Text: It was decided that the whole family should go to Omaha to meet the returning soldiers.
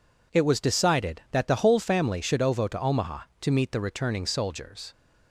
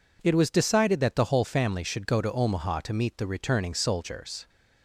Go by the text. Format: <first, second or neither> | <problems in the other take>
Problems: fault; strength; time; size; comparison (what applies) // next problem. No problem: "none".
second | says "ovo" for "go"; at 2.4 s